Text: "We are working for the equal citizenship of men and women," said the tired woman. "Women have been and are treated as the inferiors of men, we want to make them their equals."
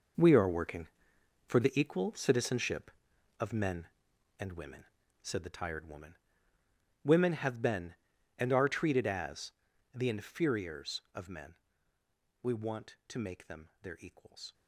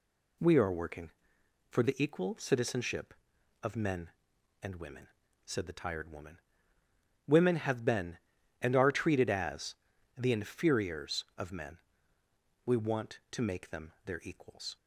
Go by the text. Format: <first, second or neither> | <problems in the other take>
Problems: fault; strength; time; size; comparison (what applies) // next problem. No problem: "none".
second | gets quieter; strong; throughout; 12 dB // pauses between "as" and "the"; at 9.5 s; 0.42 s long; also in the second